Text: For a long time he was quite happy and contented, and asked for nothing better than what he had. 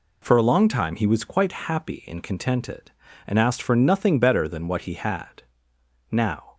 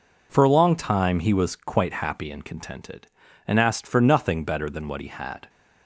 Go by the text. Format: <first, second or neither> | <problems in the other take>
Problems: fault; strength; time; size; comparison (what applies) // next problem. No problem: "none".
second | goes on to say "Now"; slight; from 6.1 s on; 0.42 s long